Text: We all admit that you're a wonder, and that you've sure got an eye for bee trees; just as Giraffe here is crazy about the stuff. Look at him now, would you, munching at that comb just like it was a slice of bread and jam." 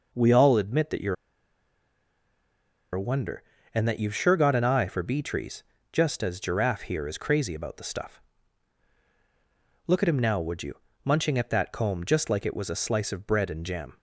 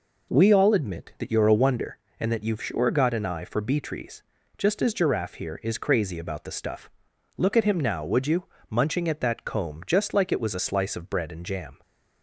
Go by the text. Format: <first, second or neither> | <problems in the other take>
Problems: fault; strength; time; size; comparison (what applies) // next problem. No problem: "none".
second | pauses between "you're" and "a"; strong; at 1.1 s; 1.8 s long